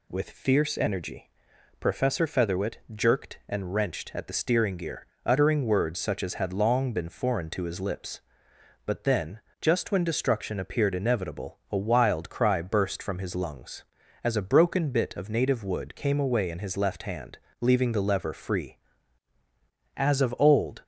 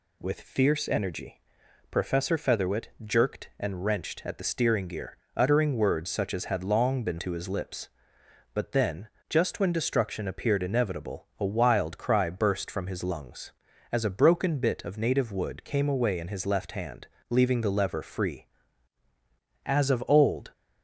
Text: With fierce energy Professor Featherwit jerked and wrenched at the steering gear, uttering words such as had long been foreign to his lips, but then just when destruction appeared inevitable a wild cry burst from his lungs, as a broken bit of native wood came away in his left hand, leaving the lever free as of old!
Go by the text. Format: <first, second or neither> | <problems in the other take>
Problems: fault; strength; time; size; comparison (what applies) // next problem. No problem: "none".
first | pauses between "energy" and "Professor"; noticeable; at 1.4 s; 0.52 s long; noticeable in the first // pauses between "Featherwit" and "jerked"; slight; at 2.8 s; 0.16 s long; slight in the first // skips "foreign"; at 7.1 s // pauses between "then" and "just"; slight; at 9.0 s; 0.20 s long; slight in the first